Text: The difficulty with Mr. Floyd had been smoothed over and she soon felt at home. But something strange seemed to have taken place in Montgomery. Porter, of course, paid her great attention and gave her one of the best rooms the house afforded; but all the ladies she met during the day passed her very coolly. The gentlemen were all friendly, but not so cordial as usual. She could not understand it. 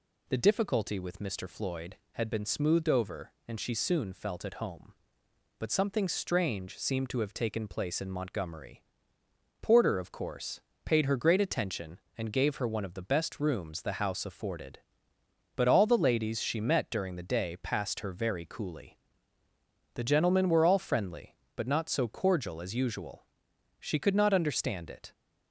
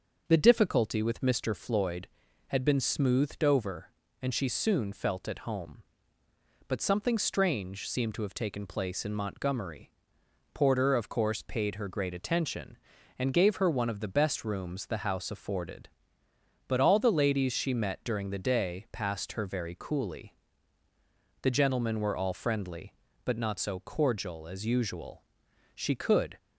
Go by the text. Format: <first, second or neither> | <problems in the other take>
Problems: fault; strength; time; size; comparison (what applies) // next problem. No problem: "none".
first | starts louder than the rest; until 1.2 s; 6.5 dB // stops before "not understand it"; at 26.3 s